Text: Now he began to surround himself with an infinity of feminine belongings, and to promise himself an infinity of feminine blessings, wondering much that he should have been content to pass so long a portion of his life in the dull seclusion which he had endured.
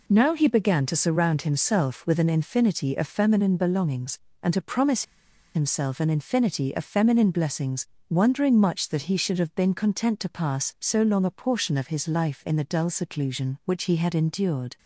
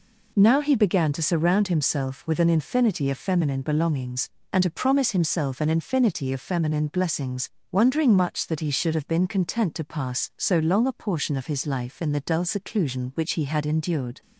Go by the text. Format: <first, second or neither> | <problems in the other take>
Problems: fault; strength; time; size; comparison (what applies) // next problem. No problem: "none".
second | pauses between "promise" and "himself"; noticeable; at 5.0 s; 0.52 s long